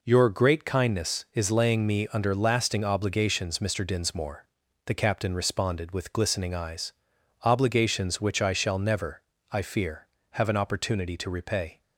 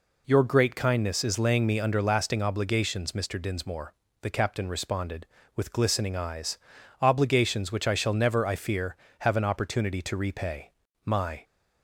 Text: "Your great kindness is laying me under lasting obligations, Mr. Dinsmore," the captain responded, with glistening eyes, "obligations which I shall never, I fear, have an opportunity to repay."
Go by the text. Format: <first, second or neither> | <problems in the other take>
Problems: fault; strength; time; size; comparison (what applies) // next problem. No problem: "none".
first | goes on to say "My"; slight; from 11.0 s on; 0.40 s long